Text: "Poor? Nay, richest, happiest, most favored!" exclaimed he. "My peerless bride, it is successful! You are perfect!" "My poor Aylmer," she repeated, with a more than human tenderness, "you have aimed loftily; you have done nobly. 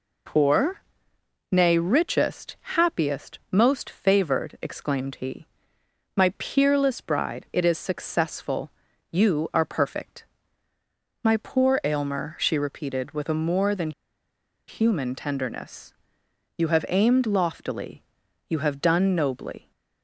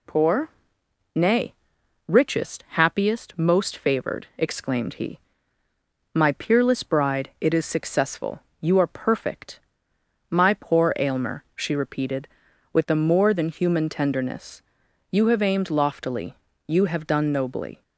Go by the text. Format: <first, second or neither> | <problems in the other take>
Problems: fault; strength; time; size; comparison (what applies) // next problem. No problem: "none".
second | pauses between "than" and "human"; noticeable; at 13.9 s; 0.77 s long